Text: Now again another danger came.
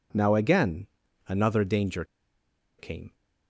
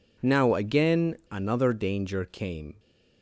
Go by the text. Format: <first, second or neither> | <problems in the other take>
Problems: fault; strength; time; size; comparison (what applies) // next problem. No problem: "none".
second | pauses between "again" and "another"; at 0.8 s; 0.40 s long; slight in the second // pauses between "danger" and "came"; noticeable; at 2.0 s; 0.75 s long